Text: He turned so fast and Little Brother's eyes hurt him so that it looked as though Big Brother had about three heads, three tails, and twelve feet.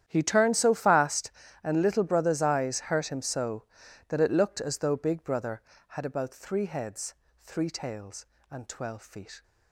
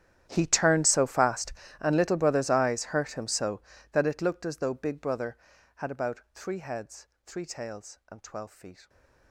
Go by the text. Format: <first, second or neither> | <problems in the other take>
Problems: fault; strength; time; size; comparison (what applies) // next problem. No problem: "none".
first | gets quieter; strong; throughout; 22 dB // starts louder than the rest; strong; until 1.3 s; 10.5 dB; strong in the first // pauses between "about" and "three"; slight; at 6.1 s; 0.15 s long